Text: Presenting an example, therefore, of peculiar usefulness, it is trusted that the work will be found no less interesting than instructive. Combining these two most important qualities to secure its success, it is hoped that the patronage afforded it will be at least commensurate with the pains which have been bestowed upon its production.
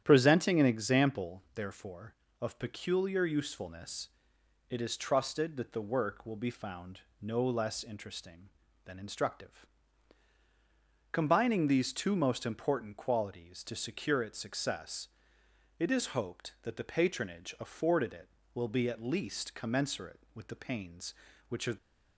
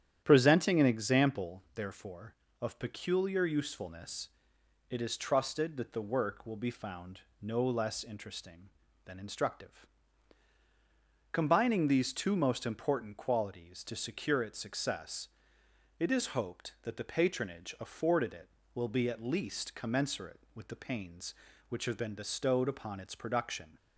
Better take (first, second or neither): second